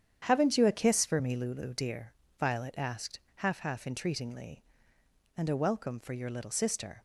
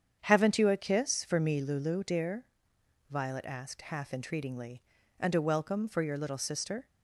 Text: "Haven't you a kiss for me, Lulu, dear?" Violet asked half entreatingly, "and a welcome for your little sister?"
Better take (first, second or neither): second